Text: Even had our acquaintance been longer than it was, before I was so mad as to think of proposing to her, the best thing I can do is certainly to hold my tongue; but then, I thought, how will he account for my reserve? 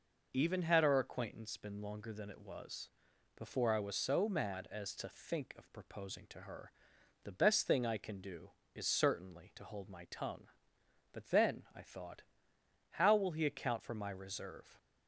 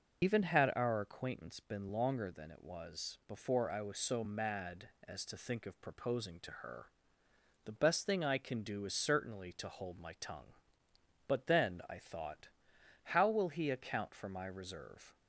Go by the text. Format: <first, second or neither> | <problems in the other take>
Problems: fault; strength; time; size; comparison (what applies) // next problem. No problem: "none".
first | loses the start of "Even"; at 0.2 s; 65 ms